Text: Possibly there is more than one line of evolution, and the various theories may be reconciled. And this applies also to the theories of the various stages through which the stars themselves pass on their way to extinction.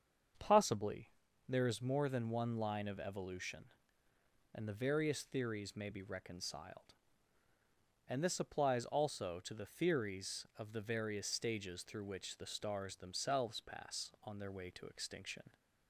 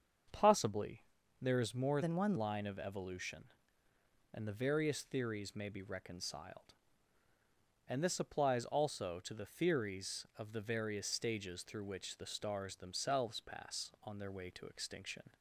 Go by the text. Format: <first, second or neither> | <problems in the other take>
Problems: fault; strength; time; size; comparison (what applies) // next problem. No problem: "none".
first | starts louder than the rest; until 1.6 s; 7 dB; strong in the first // pauses between "Possibly" and "there"; at 1.0 s; 0.38 s long; also in the first // changes voice from "than" to "one"; from 2.0 to 2.3 s; 0.3 s long